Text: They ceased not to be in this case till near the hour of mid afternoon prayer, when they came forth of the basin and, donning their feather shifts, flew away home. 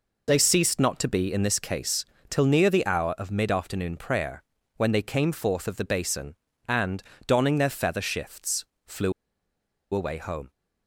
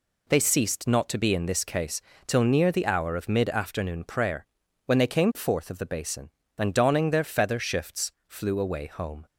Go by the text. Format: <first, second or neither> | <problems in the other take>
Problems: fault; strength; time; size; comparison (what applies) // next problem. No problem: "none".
second | pauses between "case" and "till"; slight; at 2.0 s; 0.24 s long; slight in the second // pauses between "flew" and "away"; noticeable; at 9.1 s; 0.81 s long